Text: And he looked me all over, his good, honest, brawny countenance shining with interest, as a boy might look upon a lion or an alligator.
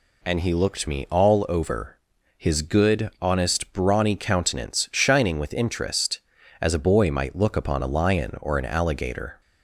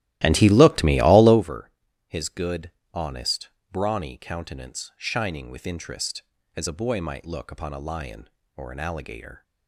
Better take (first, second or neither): first